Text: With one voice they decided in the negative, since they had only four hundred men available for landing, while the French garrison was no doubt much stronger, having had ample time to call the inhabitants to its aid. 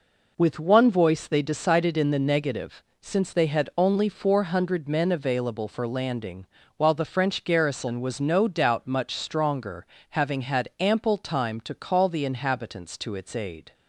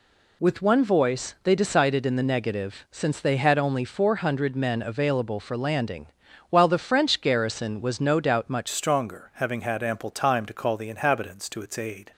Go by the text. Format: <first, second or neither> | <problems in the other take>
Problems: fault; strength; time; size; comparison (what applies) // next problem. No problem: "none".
first | changes voice at "stronger"; from 8.6 s on; 3.5 s long